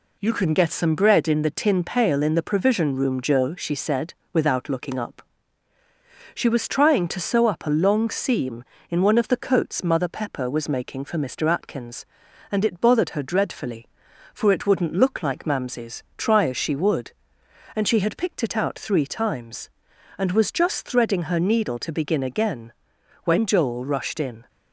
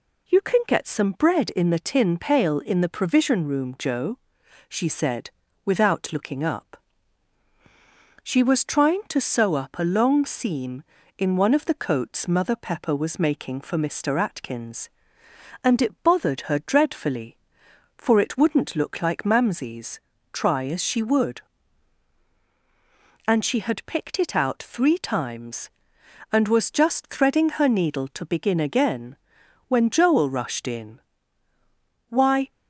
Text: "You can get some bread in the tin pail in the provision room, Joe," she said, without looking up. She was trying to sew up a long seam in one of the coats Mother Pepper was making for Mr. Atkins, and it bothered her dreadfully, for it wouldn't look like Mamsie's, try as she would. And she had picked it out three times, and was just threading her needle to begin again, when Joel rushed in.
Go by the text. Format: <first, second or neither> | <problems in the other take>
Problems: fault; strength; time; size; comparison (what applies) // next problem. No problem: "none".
first | goes on to say "Why"; slight; from 32.0 s on; 0.42 s long